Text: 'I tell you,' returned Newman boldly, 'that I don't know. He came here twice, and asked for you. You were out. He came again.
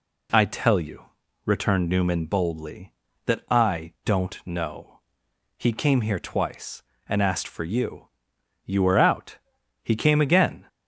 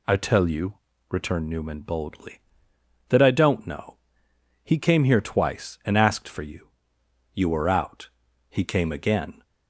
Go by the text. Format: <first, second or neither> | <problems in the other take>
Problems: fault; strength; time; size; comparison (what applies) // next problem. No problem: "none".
neither | none